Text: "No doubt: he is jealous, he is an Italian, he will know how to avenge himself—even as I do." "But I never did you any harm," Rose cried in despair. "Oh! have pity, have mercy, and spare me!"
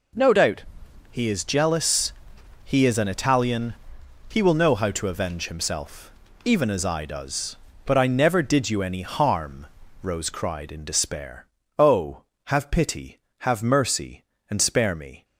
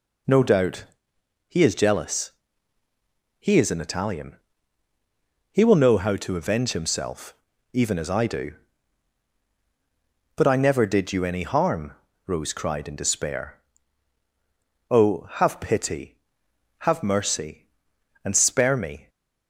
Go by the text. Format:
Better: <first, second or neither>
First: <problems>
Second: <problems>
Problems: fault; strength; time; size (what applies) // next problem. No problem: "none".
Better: second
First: says "does" for "do"; at 7.0 s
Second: none